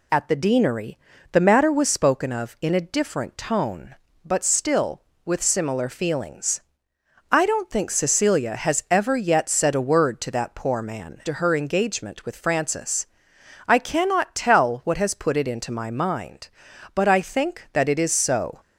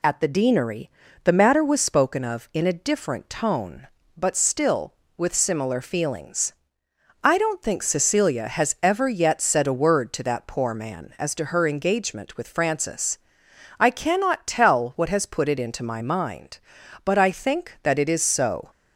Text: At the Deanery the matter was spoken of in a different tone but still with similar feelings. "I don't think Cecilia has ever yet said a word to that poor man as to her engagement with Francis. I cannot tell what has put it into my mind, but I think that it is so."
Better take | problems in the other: second | pauses between "Deanery" and "the"; slight; at 0.9 s; 0.34 s long; slight in the second // skips "as"; at 11.2 s

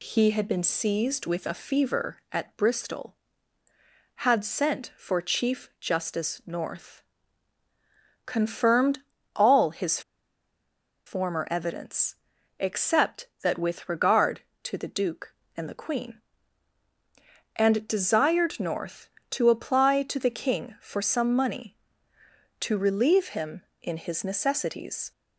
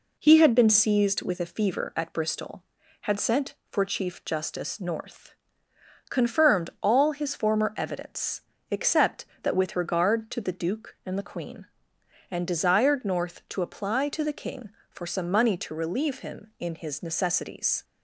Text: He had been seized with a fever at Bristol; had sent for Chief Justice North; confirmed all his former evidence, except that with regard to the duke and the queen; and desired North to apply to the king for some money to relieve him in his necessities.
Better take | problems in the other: second | pauses between "confirmed" and "all"; slight; at 9.0 s; 0.32 s long // pauses between "his" and "former"; at 10.0 s; 1.0 s long

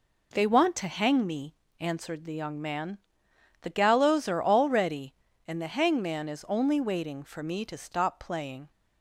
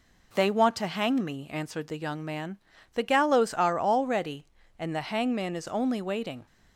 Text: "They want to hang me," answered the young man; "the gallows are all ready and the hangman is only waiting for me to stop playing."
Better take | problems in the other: first | stops before "for me to stop playing"; at 6.4 s

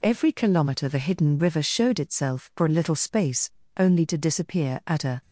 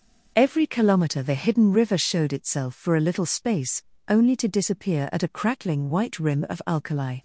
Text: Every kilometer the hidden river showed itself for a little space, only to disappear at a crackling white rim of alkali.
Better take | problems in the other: second | stops before "crackling white rim of alkali"; at 5.2 s

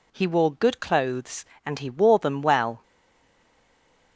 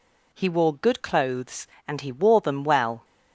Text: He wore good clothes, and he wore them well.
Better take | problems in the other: second | stays silent after the last word; noticeable; from 2.8 s on; 1.3 s long

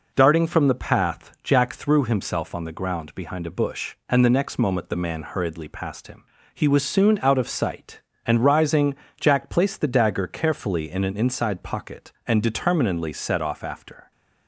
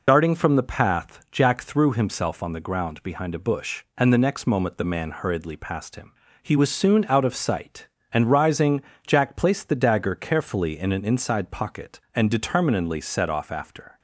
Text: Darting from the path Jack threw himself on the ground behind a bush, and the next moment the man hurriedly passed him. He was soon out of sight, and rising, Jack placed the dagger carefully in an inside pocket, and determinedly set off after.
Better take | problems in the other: first | loses the start of "Darting"; at 0.0 s; 55 ms

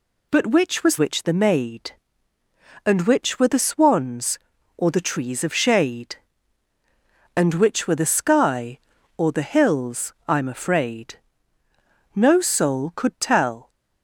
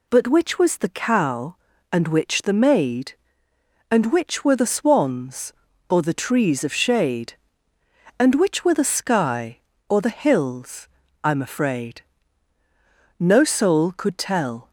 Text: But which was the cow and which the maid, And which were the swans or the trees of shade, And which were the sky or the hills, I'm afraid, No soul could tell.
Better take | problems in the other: second | skips "the cow and"; at 0.9 s

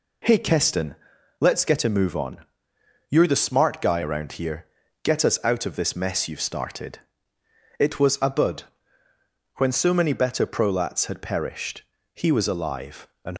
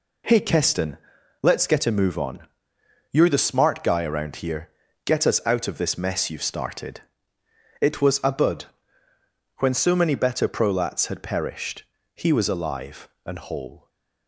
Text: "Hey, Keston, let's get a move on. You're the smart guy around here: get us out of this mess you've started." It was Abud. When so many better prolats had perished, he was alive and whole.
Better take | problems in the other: second | stops before "whole"; at 13.3 s

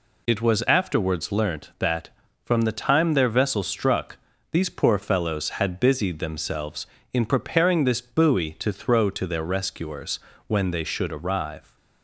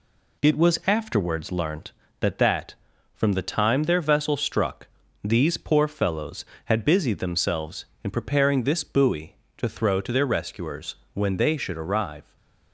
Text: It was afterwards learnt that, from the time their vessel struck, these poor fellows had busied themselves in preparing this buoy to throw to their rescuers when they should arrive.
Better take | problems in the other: first | says "that" twice; at 2.3 s // pauses between "rescuers" and "when"; slight; at 10.9 s; 0.20 s long; slight in the first // stays silent after the last word; slight; from 12.2 s on; 0.5 s long

